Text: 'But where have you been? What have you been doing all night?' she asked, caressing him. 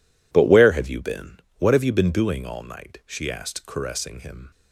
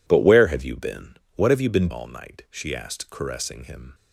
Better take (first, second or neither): first